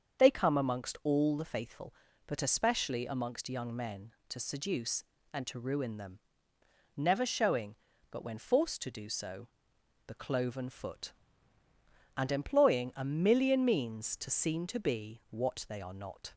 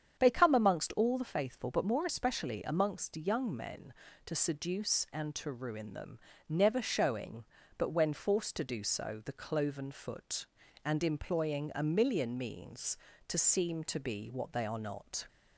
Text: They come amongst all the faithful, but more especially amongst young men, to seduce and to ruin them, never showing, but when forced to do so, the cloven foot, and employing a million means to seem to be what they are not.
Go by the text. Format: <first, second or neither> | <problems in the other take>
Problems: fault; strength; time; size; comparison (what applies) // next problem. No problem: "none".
second | starts louder than the rest; until 1.2 s; 7 dB; strong in the second // skips "more"; at 2.4 s